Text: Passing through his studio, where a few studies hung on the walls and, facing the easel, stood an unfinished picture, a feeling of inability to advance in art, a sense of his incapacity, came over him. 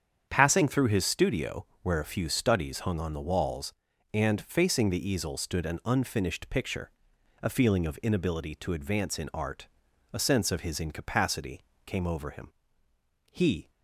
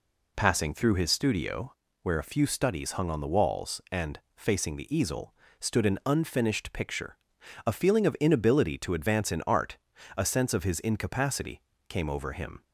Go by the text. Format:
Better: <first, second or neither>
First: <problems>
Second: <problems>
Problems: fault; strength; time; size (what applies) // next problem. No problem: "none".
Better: second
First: starts louder than the rest; strong; until 1.3 s; 8 dB // goes on to say "He"; slight; from 13.3 s on; 0.38 s long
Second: none